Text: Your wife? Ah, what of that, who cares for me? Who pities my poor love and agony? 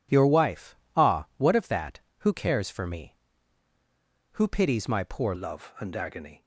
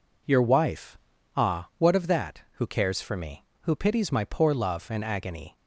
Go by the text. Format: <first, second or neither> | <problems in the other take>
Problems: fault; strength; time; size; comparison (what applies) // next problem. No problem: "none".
second | changes voice at "love"; from 5.3 s on; 1.1 s long